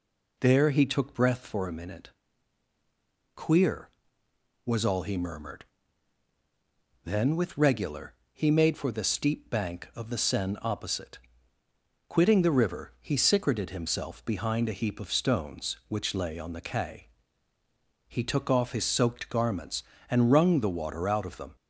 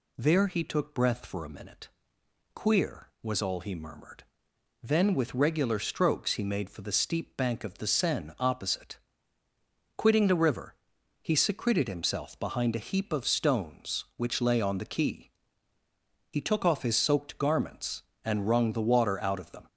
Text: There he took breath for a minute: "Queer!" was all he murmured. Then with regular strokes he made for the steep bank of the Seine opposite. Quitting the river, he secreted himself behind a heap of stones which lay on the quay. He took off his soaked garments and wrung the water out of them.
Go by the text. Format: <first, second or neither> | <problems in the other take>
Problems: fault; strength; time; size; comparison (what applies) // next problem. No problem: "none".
second | skips "strokes"; at 8.2 s